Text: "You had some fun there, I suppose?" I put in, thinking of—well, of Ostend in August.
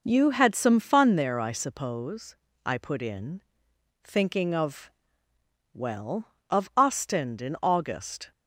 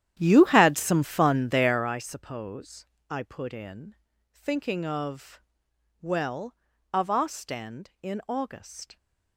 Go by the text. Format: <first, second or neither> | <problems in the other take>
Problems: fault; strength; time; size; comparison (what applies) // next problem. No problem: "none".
first | starts louder than the rest; strong; until 1.9 s; 11 dB